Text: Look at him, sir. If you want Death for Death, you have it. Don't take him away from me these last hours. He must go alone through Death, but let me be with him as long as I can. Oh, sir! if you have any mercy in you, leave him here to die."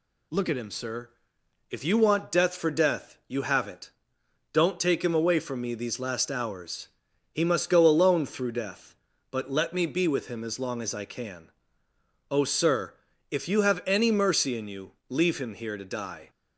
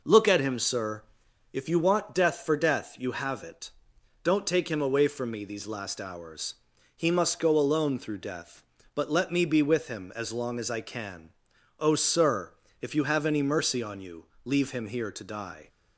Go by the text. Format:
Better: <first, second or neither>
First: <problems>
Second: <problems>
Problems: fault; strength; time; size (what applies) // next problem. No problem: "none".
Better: first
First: none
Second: says "on" for "in"; at 13.8 s